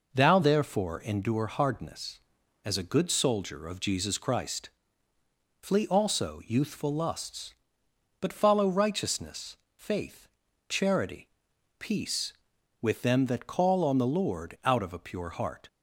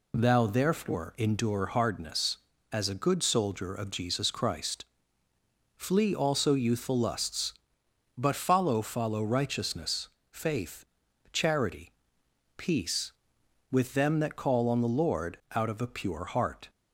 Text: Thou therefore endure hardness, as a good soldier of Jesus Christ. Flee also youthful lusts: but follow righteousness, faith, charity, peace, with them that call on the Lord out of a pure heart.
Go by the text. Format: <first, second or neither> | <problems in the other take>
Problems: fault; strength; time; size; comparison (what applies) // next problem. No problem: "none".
first | says "follow" twice; at 8.8 s // pauses between "Lord" and "out"; slight; at 15.3 s; 0.16 s long